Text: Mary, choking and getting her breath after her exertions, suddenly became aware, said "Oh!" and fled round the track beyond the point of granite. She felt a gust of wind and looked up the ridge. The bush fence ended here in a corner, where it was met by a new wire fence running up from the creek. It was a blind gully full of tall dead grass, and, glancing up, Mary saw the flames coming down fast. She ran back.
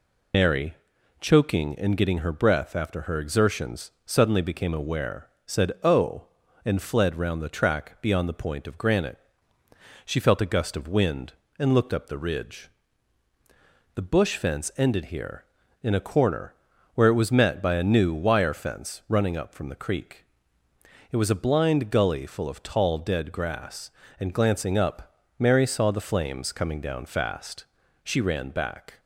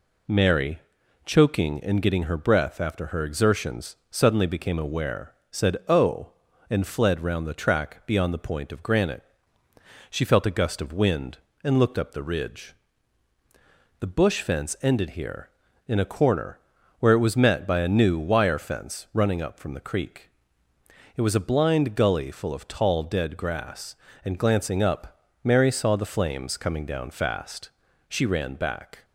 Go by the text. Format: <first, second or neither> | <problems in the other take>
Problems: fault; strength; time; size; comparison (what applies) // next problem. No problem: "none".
second | loses the start of "Mary"; at 0.3 s; 110 ms